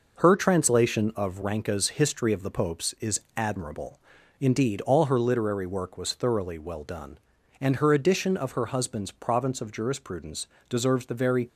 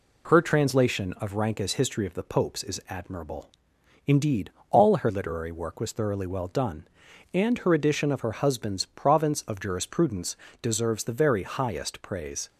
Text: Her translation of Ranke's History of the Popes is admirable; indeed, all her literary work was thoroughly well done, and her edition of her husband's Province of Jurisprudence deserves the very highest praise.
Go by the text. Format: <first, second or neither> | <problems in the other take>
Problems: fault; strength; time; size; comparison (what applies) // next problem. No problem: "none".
second | pauses between "is" and "admirable"; slight; at 3.2 s; 0.16 s long // pauses between "Jurisprudence" and "deserves"; slight; at 10.4 s; 0.20 s long; slight in the second // stops before "highest praise"; at 11.4 s